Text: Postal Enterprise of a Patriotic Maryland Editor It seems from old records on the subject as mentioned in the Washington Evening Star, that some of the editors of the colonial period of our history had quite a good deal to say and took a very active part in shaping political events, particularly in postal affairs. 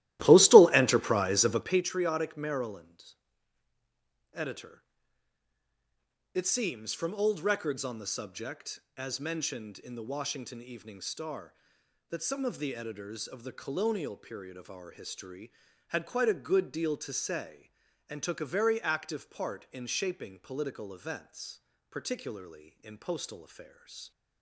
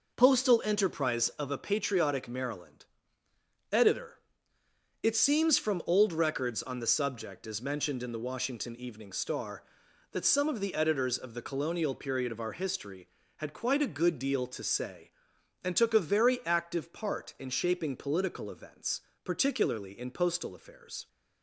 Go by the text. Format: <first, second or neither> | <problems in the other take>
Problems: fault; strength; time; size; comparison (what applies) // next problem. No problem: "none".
second | starts louder than the rest; strong; until 1.8 s; 15 dB // pauses between "Maryland" and "Editor"; at 3.1 s; 1.2 s long; noticeable in the second // pauses between "Editor" and "It"; strong; at 4.8 s; 1.5 s long; noticeable in the second